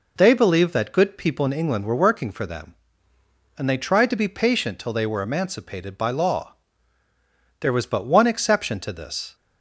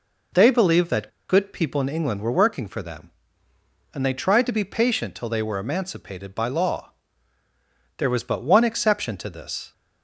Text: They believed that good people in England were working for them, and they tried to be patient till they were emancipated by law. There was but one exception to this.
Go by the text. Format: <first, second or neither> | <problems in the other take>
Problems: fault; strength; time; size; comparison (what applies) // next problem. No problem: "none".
first | pauses between "that" and "good"; slight; at 1.0 s; 0.19 s long